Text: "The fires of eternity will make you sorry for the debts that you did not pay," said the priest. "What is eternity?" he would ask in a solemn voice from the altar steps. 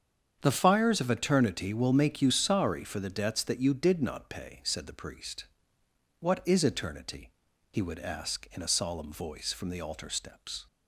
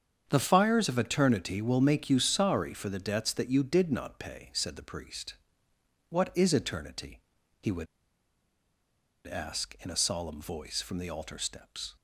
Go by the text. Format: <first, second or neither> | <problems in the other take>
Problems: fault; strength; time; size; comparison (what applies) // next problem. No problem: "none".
first | starts louder than the rest; strong; until 1.2 s; 7.5 dB; strong in the first // pauses between "would" and "ask"; strong; at 7.8 s; 1.4 s long